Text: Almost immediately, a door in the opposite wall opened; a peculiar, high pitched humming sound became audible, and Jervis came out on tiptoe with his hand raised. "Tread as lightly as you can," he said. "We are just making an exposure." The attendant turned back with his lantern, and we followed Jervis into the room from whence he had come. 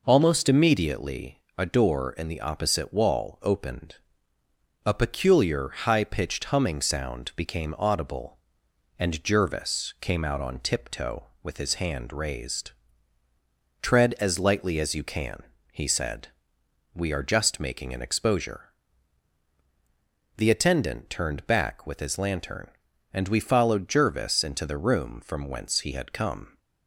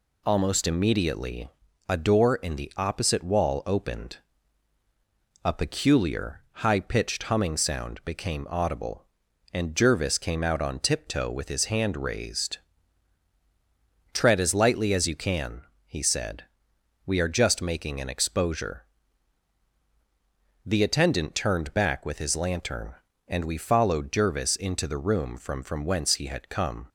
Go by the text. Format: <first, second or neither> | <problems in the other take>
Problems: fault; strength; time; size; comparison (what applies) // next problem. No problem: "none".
first | says "from" twice; at 25.6 s